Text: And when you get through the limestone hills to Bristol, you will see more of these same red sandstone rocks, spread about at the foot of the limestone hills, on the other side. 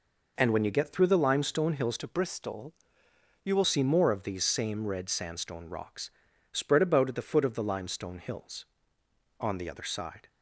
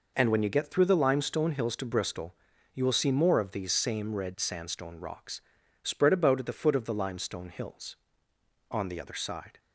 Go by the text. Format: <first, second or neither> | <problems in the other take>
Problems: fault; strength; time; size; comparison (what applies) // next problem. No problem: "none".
second | changes voice from "to" to "will"; from 1.9 to 3.6 s; 1.7 s long